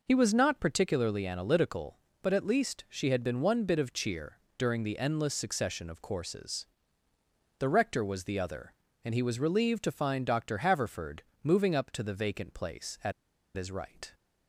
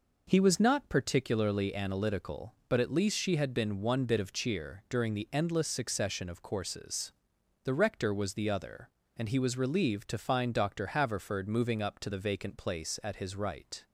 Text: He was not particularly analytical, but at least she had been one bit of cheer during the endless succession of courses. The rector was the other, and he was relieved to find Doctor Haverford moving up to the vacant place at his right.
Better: second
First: pauses between "cheer" and "during"; slight; at 4.3 s; 0.20 s long // pauses between "Haverford" and "moving"; slight; at 11.2 s; 0.22 s long // pauses between "at" and "his"; at 13.1 s; 0.43 s long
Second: none

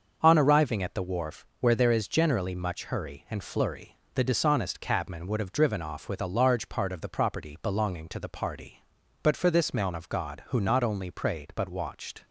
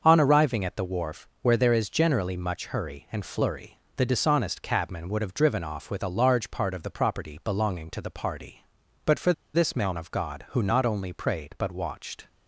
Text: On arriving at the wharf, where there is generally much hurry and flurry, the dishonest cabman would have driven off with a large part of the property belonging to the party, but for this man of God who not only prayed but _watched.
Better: first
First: starts louder than the rest; until 1.2 s; 6.5 dB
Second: starts louder than the rest; until 1.0 s; 6.5 dB // pauses between "for" and "this"; slight; at 9.3 s; 0.22 s long

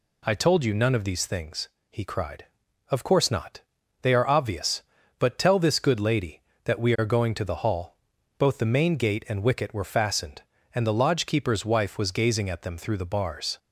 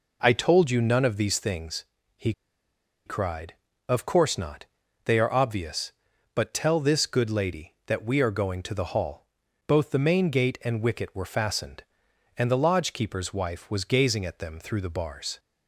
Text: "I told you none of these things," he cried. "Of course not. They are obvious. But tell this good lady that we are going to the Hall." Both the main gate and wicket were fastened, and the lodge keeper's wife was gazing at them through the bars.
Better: first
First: none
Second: pauses between "he" and "cried"; noticeable; at 2.3 s; 0.74 s long

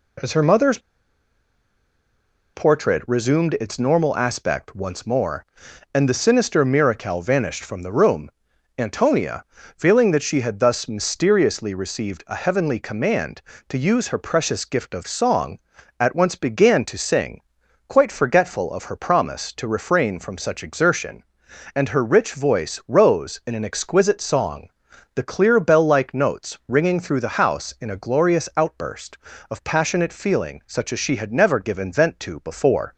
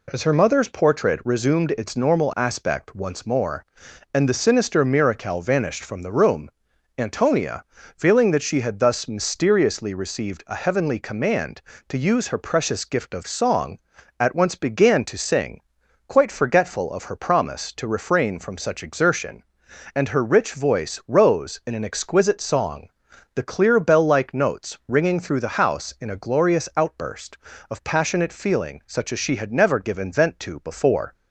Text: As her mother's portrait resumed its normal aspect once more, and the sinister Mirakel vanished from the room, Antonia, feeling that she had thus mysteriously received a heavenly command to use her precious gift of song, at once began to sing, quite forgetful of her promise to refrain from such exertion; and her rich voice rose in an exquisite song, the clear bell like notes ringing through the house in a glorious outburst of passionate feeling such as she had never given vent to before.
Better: second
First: pauses between "mother's" and "portrait"; strong; at 0.7 s; 1.7 s long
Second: none

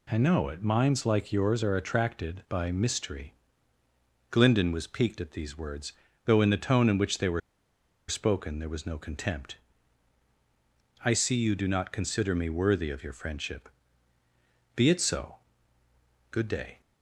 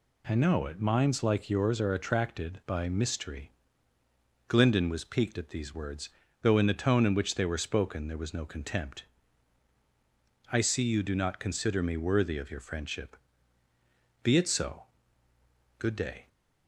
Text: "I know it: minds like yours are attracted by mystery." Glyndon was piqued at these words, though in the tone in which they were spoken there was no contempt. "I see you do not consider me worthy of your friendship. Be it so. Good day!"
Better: second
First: pauses between "were" and "spoken"; noticeable; at 7.4 s; 0.68 s long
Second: none

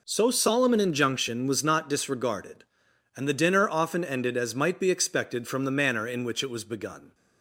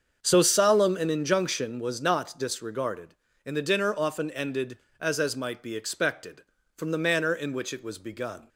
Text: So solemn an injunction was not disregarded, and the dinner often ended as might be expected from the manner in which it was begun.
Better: first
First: none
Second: starts louder than the rest; until 1.2 s; 7 dB // says "as" twice; at 5.1 s

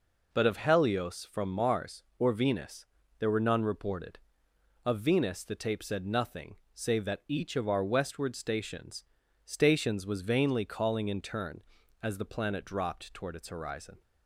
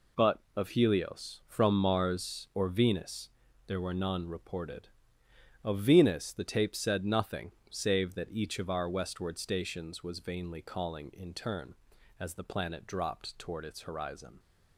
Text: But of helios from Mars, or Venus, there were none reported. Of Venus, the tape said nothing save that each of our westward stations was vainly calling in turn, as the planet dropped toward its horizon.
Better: second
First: pauses between "nothing" and "save"; slight; at 6.5 s; 0.18 s long // says "stations" twice; at 9.4 s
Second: pauses between "nothing" and "save"; slight; at 7.5 s; 0.18 s long

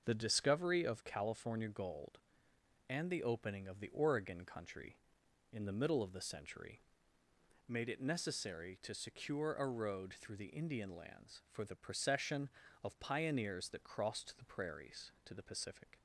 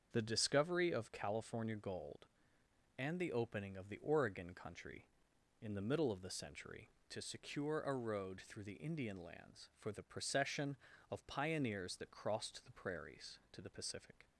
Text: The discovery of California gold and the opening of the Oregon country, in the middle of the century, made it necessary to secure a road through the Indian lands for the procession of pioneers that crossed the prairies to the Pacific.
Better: first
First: starts louder than the rest; until 1.0 s; 6.5 dB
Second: starts louder than the rest; strong; until 1.1 s; 7 dB // skips "made it necessary"; at 6.9 s

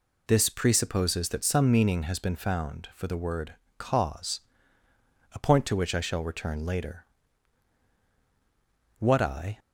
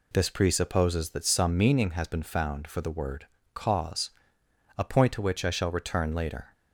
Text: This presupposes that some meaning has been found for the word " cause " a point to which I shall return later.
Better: second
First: goes on to say "What I"; from 9.0 s on; 0.58 s long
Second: none

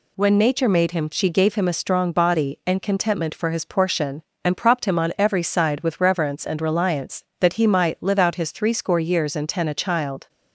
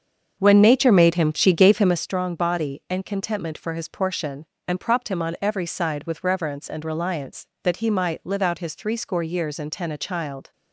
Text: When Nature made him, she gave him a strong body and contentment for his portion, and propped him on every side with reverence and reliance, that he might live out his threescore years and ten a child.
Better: first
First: none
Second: starts louder than the rest; until 2.0 s; 7 dB

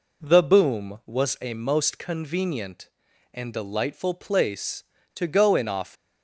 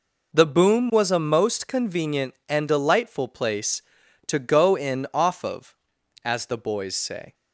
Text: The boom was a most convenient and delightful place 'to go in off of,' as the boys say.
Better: second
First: stops before "of as the boys say"; at 5.9 s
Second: none

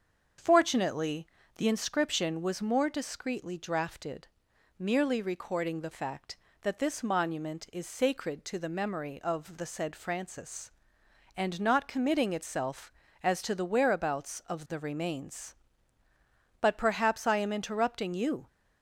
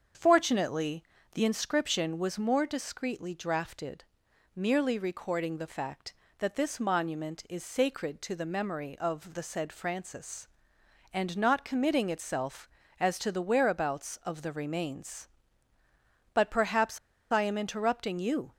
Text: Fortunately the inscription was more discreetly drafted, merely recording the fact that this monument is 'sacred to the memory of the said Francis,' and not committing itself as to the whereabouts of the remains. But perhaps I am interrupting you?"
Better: first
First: starts louder than the rest; until 1.7 s; 7 dB // pauses between "Fortunately" and "the"; slight; at 1.2 s; 0.30 s long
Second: starts louder than the rest; until 1.4 s; 7 dB // pauses between "Fortunately" and "the"; slight; at 1.0 s; 0.30 s long // pauses between "perhaps" and "I"; slight; at 16.9 s; 0.32 s long

